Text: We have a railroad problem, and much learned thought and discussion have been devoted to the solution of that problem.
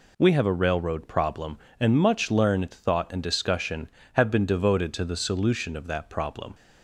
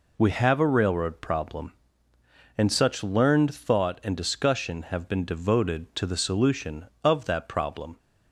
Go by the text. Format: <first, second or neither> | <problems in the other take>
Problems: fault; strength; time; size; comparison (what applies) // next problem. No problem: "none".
first | says "such" for "much"; at 2.7 s